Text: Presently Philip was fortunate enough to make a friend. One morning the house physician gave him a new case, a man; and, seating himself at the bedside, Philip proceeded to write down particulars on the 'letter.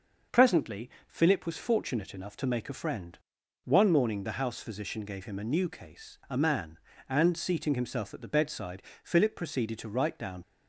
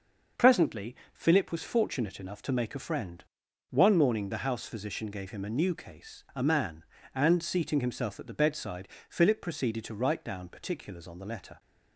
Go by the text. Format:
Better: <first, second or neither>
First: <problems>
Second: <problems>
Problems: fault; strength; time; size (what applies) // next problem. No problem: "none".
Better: second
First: starts louder than the rest; noticeable; until 1.5 s; 6 dB // pauses between "Presently" and "Philip"; slight; at 0.8 s; 0.18 s long // stops before "particulars on the letter"; at 10.4 s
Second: starts louder than the rest; noticeable; until 1.5 s; 6 dB // pauses between "Presently" and "Philip"; slight; at 0.9 s; 0.18 s long